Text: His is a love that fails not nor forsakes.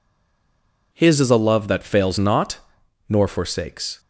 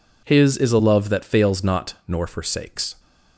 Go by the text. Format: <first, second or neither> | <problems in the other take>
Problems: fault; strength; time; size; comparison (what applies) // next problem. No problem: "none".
second | stays silent before the first word; slight; until 0.9 s; 0.9 s long // pauses between "not" and "nor"; noticeable; at 2.5 s; 0.50 s long